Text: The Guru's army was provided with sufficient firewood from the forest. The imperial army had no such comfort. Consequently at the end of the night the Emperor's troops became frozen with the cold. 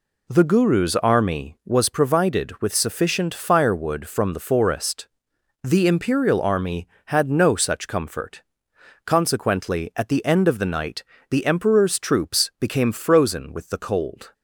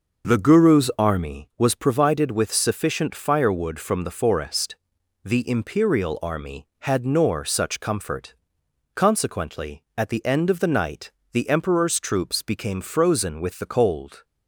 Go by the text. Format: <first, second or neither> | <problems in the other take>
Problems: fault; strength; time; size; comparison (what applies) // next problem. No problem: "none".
first | says "nor" for "no"; at 7.0 s // pauses between "night" and "the"; slight; at 11.1 s; 0.20 s long; slight in the first